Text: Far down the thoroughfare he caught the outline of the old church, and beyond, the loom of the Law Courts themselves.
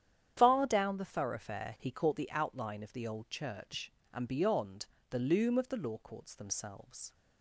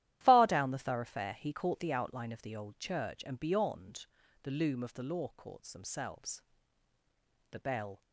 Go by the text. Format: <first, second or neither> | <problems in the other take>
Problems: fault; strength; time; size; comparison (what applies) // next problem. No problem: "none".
first | starts louder than the rest; strong; until 1.2 s; 13 dB; strong in the first // goes on to say "The bell"; from 7.5 s on; 0.50 s long